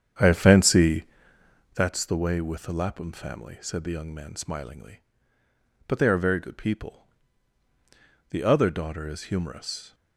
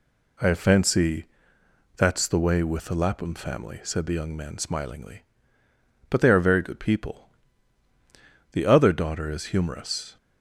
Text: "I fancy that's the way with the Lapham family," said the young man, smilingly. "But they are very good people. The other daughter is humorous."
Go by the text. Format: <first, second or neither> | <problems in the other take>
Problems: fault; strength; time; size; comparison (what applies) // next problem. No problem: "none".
second | starts louder than the rest; strong; until 1.8 s; 8.5 dB // pauses between "fancy" and "that's"; noticeable; at 1.0 s; 0.70 s long; noticeable in the second